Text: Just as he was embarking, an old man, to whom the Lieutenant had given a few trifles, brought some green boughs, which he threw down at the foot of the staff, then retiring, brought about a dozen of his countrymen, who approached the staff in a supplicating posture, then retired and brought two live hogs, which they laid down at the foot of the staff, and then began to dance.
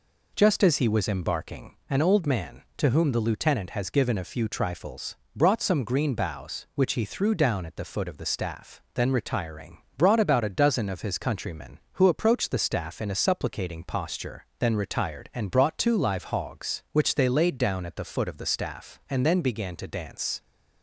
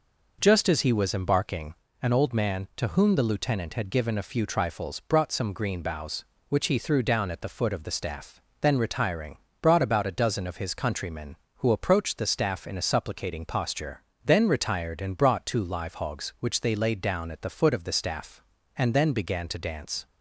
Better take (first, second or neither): second